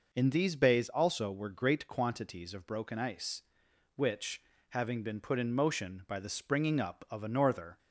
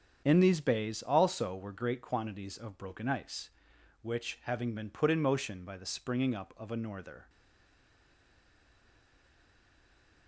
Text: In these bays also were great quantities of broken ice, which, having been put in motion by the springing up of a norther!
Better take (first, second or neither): first